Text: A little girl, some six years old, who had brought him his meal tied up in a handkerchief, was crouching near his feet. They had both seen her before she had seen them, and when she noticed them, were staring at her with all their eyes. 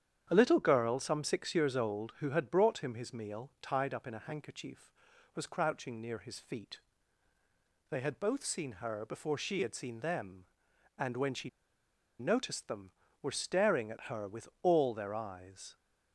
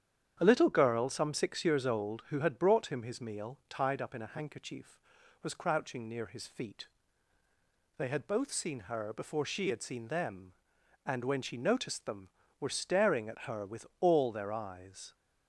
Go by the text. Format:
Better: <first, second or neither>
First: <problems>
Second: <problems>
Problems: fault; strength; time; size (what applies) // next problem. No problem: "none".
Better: second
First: starts louder than the rest; strong; until 1.3 s; 9 dB // pauses between "she" and "noticed"; noticeable; at 11.4 s; 0.70 s long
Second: starts louder than the rest; strong; until 1.4 s; 9 dB